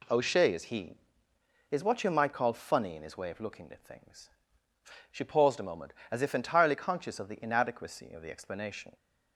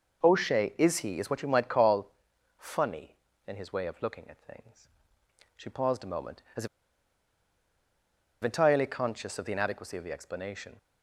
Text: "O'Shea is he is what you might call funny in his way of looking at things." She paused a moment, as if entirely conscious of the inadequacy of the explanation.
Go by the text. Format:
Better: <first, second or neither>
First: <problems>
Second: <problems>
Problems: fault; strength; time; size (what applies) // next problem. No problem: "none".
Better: first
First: none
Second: pauses between "call" and "funny"; noticeable; at 2.1 s; 0.46 s long // pauses between "as" and "if"; strong; at 6.6 s; 1.7 s long